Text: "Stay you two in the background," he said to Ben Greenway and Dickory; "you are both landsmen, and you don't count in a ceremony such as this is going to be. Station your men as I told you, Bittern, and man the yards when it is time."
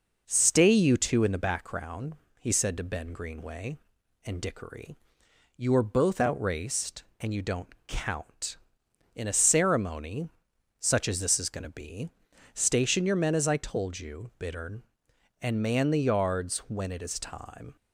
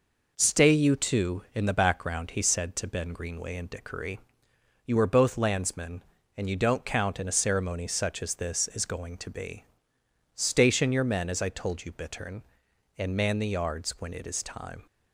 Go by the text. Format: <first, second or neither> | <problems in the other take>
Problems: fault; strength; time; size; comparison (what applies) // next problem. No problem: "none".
second | says "outraced" for "landsmen"; at 6.2 s // pauses between "ceremony" and "such"; noticeable; at 10.2 s; 0.52 s long